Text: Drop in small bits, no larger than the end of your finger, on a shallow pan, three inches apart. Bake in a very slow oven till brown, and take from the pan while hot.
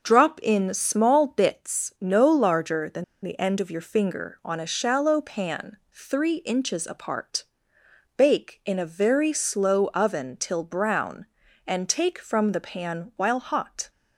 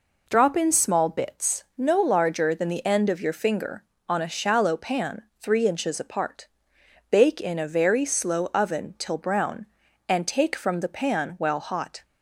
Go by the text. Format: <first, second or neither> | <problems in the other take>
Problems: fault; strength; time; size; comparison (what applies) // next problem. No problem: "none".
second | pauses between "than" and "the"; slight; at 3.0 s; 0.19 s long